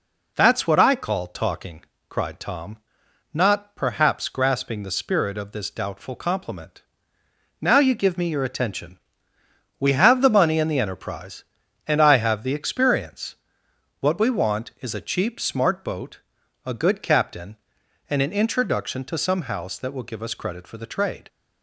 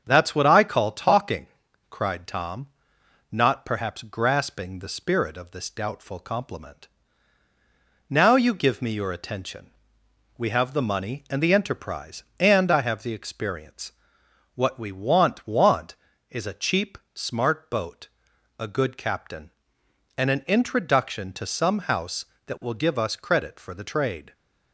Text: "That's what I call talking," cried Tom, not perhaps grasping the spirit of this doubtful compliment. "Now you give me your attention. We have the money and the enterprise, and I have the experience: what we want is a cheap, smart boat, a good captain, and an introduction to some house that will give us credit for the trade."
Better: first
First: none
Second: starts louder than the rest; until 1.0 s; 7 dB // says "want" twice; at 15.4 s

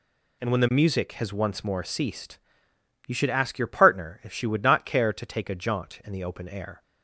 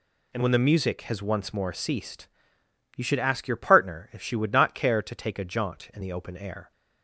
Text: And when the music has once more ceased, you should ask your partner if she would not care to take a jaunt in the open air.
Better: neither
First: none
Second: none

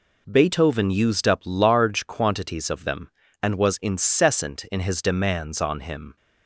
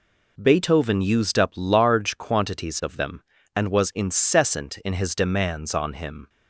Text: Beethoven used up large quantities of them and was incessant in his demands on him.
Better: neither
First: none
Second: none

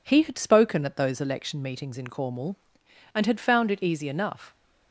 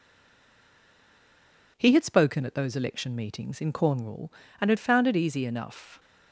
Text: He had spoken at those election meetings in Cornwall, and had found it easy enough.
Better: first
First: none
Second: stays silent before the first word; noticeable; until 1.7 s; 1.7 s long

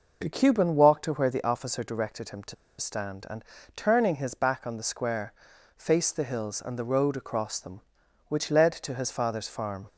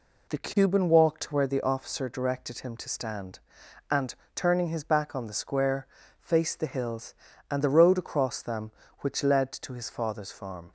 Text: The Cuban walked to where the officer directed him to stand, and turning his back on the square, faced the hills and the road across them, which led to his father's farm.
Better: second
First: pauses between "to" and "stand"; slight; at 2.5 s; 0.24 s long // pauses between "and" and "turning"; slight; at 3.4 s; 0.30 s long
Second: pauses between "and" and "turning"; slight; at 4.1 s; 0.22 s long

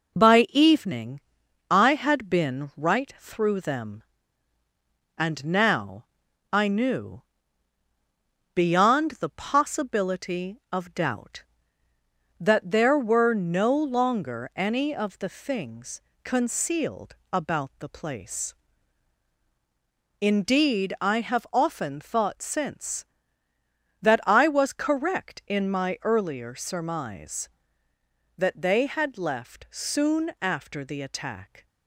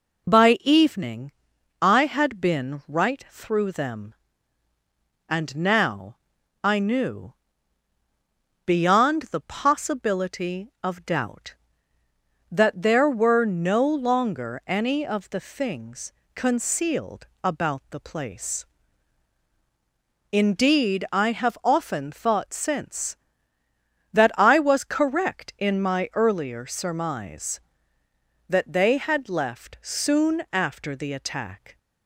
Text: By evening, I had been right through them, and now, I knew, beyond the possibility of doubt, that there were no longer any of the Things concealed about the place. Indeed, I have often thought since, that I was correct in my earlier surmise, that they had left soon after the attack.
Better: second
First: gets quieter; noticeable; throughout; 4 dB // pauses between "Things" and "concealed"; slight; at 16.0 s; 0.22 s long // pauses between "concealed" and "about"; slight; at 17.1 s; 0.18 s long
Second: pauses between "Things" and "concealed"; slight; at 16.1 s; 0.22 s long // pauses between "concealed" and "about"; slight; at 17.2 s; 0.18 s long

